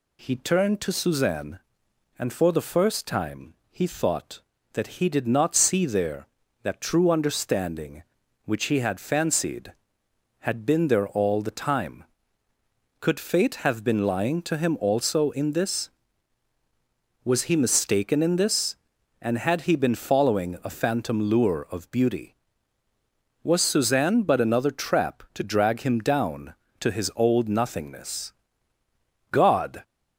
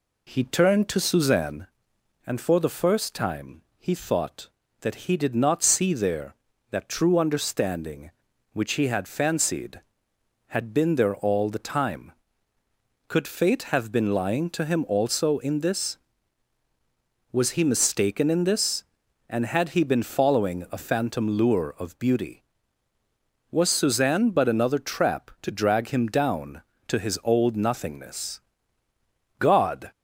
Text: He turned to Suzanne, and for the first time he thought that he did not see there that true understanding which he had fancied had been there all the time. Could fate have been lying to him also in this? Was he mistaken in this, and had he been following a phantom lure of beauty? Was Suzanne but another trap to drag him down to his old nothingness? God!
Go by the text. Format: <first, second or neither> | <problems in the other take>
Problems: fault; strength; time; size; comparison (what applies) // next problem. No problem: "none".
first | starts louder than the rest; slight; until 1.6 s; 2.5 dB // pauses between "time" and "he"; slight; at 3.6 s; 0.16 s long; slight in the first